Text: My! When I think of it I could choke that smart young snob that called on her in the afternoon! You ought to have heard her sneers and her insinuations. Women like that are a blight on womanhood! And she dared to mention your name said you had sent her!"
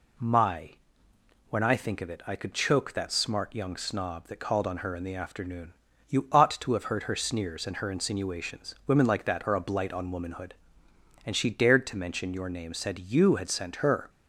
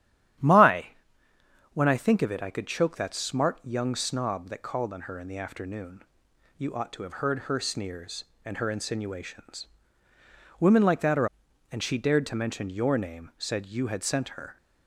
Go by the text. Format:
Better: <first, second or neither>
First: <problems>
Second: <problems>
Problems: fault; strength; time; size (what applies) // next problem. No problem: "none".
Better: first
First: none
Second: starts louder than the rest; strong; until 2.2 s; 11.5 dB // skips "a blight on womanhood"; at 11.4 s